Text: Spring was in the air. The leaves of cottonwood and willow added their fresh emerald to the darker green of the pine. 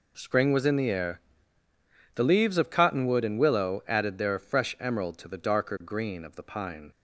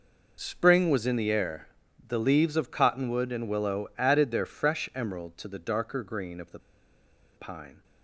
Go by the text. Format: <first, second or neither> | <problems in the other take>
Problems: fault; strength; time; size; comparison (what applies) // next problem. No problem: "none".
first | pauses between "the" and "pine"; noticeable; at 6.5 s; 0.77 s long